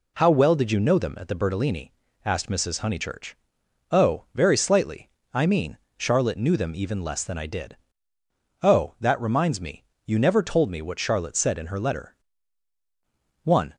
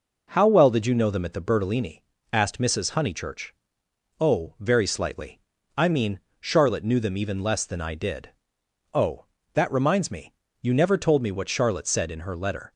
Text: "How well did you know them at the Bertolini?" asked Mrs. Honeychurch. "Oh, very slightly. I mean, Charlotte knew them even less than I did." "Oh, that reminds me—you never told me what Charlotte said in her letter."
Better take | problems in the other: second | goes on to say "One"; slight; from 13.4 s on; 0.32 s long

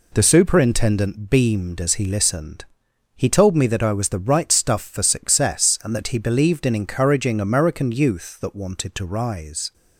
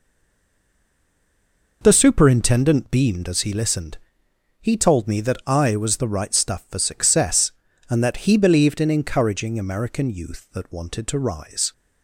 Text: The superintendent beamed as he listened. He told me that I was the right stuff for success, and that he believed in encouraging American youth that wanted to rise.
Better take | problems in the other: first | stays silent before the first word; noticeable; until 1.8 s; 1.8 s long

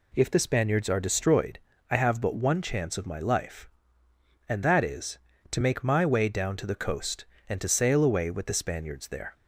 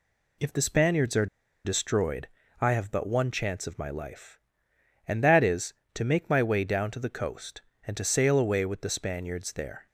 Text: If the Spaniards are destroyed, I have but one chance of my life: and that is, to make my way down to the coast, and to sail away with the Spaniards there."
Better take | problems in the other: first | pauses between "are" and "destroyed"; at 1.2 s; 0.38 s long

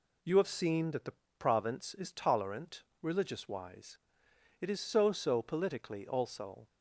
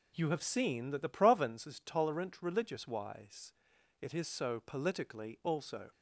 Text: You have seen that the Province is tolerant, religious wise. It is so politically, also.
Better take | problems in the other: second | pauses between "the" and "Province"; slight; at 1.1 s; 0.24 s long // says "so" twice; at 5.1 s

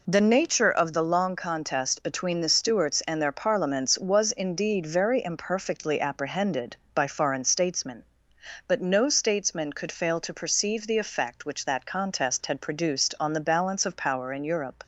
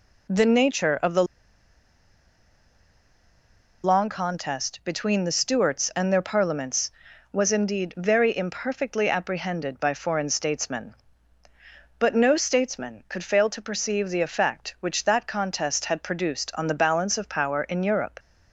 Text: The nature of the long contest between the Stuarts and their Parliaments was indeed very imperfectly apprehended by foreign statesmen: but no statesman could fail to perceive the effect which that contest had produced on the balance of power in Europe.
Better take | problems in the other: first | pauses between "the" and "long"; strong; at 1.2 s; 2.6 s long

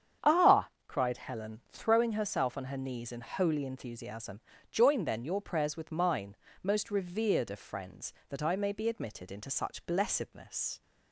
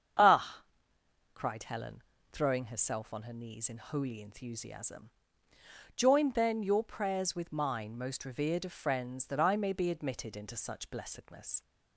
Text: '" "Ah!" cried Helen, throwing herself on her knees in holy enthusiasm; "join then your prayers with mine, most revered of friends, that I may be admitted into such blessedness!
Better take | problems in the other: neither | starts louder than the rest; strong; the same in both

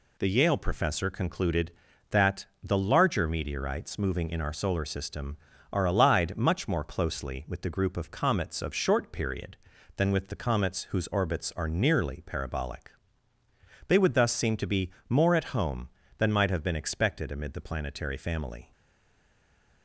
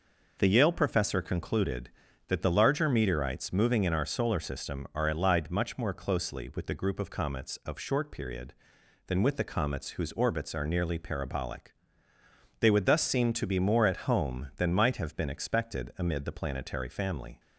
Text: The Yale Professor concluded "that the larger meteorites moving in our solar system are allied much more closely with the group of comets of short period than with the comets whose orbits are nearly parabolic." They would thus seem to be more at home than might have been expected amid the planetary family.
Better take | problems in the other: second | pauses between "that" and "the"; slight; at 2.4 s; 0.18 s long // pauses between "be" and "more"; slight; at 14.8 s; 0.20 s long // stays silent after the last word; noticeable; from 18.7 s on; 1.1 s long

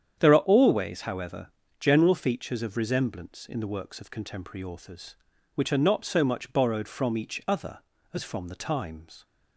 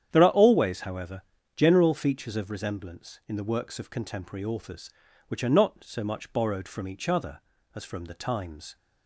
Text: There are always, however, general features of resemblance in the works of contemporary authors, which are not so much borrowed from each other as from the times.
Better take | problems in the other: neither | starts louder than the rest; strong; the same in both

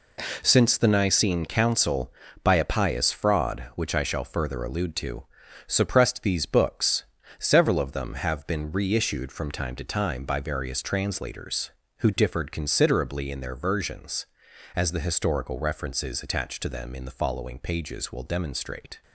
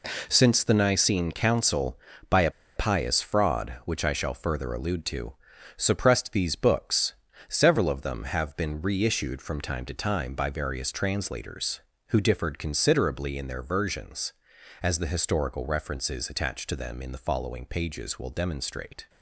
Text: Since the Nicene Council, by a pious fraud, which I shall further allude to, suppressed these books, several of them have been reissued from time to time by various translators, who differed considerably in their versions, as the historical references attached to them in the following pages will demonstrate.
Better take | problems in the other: first | pauses between "a" and "pious"; slight; at 2.5 s; 0.24 s long

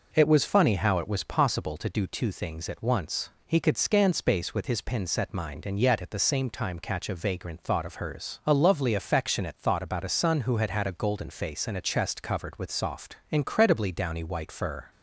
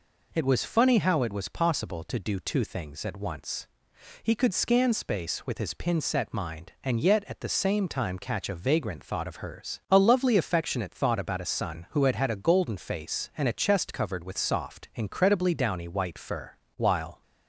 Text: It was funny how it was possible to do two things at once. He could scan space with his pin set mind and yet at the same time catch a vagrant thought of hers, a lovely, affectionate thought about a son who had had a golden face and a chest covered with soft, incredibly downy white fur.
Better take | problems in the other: first | goes on to say "While"; slight; from 16.7 s on; 0.44 s long

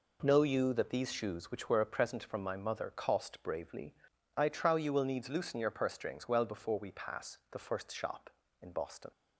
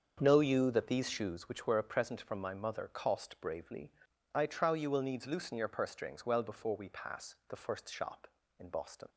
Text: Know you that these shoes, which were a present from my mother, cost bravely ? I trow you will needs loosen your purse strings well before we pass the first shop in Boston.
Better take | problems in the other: first | starts louder than the rest; until 1.4 s; 7 dB

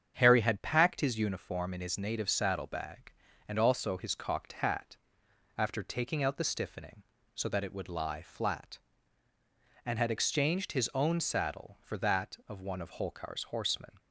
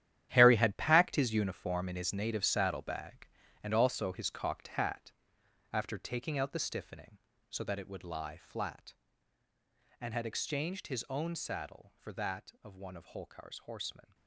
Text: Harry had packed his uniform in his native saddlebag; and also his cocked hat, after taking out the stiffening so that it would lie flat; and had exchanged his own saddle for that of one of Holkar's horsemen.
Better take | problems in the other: first | gets quieter; strong; throughout; 13 dB // starts louder than the rest; strong; until 1.3 s; 11 dB; strong in the first

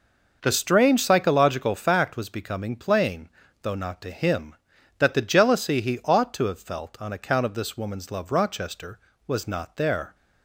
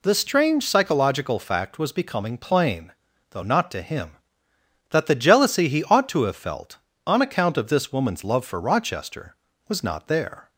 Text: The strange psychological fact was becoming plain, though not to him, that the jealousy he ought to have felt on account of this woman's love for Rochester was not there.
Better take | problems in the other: second | skips "for"; at 8.3 s

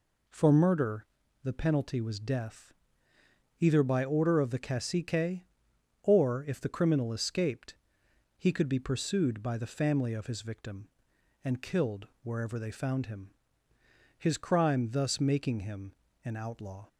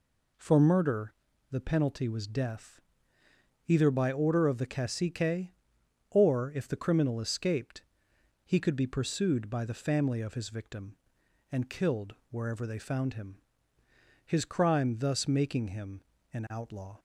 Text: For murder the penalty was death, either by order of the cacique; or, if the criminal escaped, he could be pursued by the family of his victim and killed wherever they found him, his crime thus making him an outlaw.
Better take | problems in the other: neither | pauses between "murder" and "the"; slight; the same in both // pauses between "killed" and "wherever"; slight; the same in both // pauses between "him" and "an"; slight; the same in both

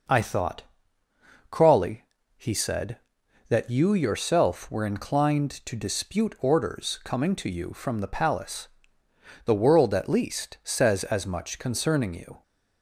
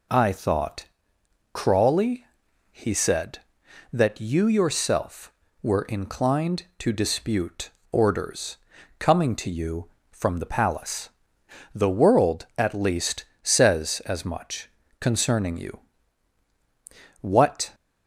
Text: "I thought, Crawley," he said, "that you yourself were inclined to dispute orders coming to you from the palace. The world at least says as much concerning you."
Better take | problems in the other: first | pauses between "dispute" and "orders"; slight; at 7.6 s; 0.24 s long // pauses between "orders" and "coming"; at 8.5 s; 0.42 s long // pauses between "least" and "says"; slight; at 13.2 s; 0.16 s long // pauses between "much" and "concerning"; slight; at 14.7 s; 0.28 s long // goes on to say "What"; from 17.2 s on; 0.54 s long

